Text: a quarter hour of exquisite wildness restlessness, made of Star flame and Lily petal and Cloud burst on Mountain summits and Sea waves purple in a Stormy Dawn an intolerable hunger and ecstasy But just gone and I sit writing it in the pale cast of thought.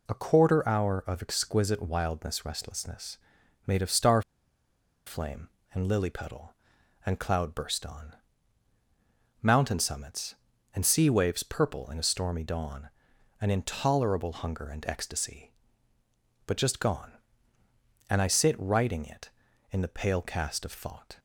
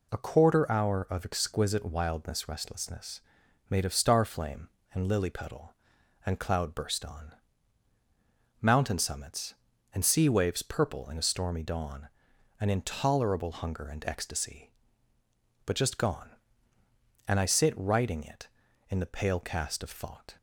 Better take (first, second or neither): second